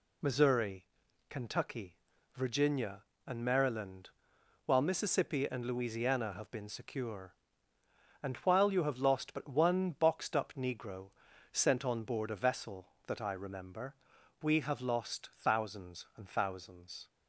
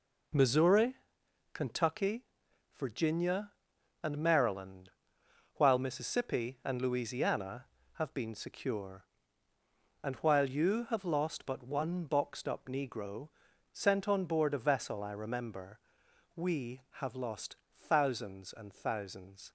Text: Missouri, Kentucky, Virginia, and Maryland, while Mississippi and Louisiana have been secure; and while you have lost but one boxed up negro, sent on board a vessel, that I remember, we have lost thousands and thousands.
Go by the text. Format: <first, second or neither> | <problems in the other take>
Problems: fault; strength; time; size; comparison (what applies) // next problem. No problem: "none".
first | skips "that"; at 15.0 s // pauses between "lost" and "thousands"; slight; at 17.5 s; 0.32 s long